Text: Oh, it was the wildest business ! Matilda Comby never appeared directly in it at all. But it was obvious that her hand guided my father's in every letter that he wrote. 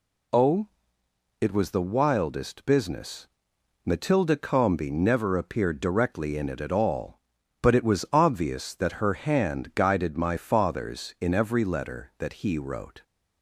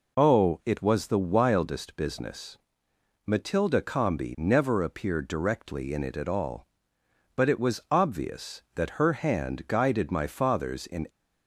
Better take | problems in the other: first | stops before "every letter that he wrote"; at 11.0 s

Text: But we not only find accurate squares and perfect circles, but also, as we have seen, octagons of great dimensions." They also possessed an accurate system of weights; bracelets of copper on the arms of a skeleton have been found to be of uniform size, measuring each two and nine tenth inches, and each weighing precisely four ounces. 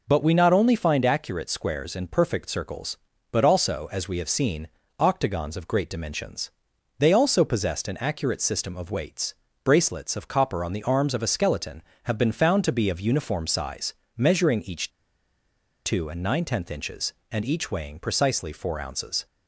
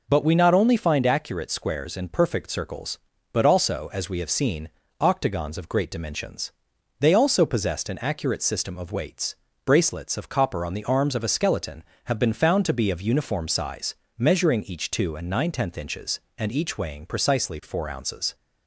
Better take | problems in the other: second | pauses between "each" and "two"; noticeable; at 14.9 s; 0.94 s long

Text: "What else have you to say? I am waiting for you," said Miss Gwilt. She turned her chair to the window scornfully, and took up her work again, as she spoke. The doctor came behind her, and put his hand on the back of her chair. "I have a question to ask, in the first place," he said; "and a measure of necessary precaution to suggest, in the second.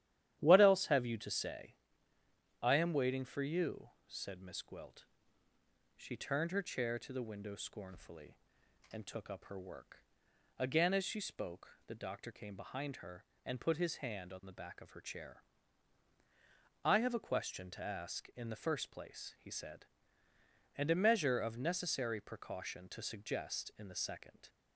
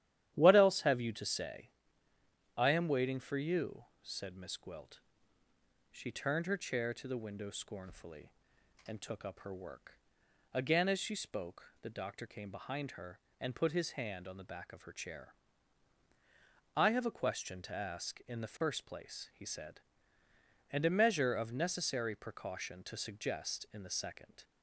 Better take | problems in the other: neither | starts louder than the rest; strong; the same in both // pauses between "work" and "again"; noticeable; the same in both

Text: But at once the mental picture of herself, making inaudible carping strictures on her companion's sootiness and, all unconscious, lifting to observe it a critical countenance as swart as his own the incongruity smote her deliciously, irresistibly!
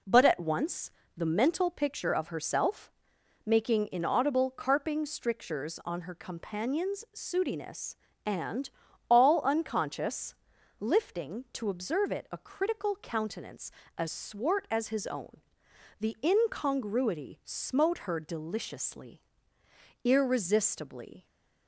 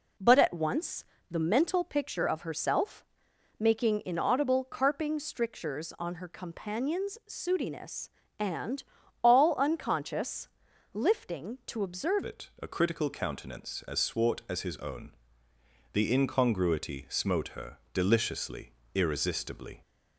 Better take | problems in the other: first | pauses between "once" and "the"; slight; at 1.0 s; 0.26 s long; slight in the first // changes voice at "it"; from 12.2 s on; 7.6 s long // pauses between "own" and "the"; noticeable; at 15.1 s; 0.82 s long; noticeable in the first // pauses between "her" and "deliciously"; slight; at 17.7 s; 0.16 s long

